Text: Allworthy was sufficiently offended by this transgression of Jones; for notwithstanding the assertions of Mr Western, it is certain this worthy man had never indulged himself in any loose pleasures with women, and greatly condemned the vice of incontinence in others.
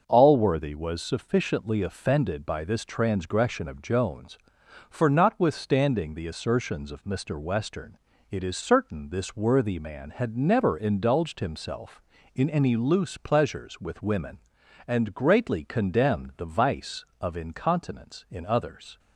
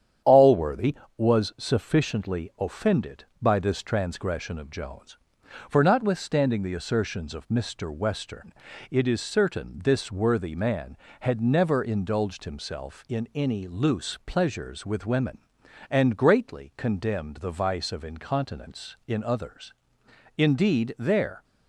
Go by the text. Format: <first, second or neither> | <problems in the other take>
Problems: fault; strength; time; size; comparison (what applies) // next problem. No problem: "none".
first | starts louder than the rest; strong; until 1.4 s; 9 dB; noticeable in the first // goes on to say "Indeed there"; noticeable; from 20.3 s on; 1.0 s long